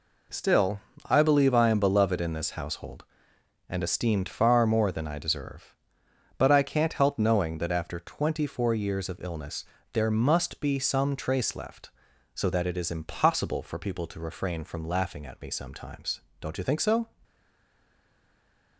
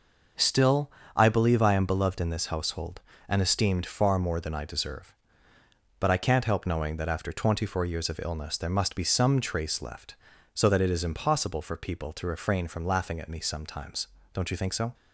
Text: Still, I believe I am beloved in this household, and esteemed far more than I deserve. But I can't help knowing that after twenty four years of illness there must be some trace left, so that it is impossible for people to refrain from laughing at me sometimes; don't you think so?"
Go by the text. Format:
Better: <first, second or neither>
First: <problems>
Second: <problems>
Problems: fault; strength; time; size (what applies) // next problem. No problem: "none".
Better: second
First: pauses between "illness" and "there"; slight; at 9.6 s; 0.28 s long // stays silent after the last word; noticeable; from 17.2 s on; 1.5 s long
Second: none